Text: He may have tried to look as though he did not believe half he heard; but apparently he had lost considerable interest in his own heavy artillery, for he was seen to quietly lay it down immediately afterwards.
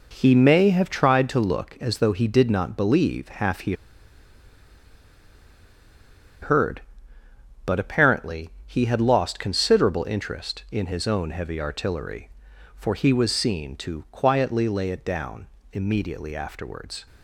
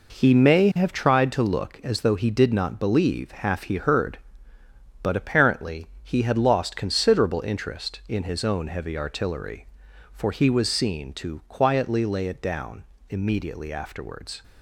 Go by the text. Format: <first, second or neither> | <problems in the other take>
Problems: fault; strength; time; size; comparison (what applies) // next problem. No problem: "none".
second | pauses between "he" and "heard"; strong; at 3.7 s; 2.6 s long // pauses between "apparently" and "he"; slight; at 8.4 s; 0.18 s long; slight in the second // pauses between "down" and "immediately"; slight; at 15.4 s; 0.26 s long; slight in the second